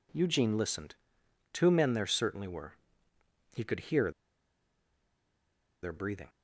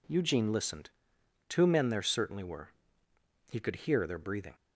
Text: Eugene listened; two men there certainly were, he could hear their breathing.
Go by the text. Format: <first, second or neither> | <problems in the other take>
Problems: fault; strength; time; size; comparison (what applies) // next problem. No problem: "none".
second | pauses between "hear" and "their"; strong; at 4.0 s; 1.7 s long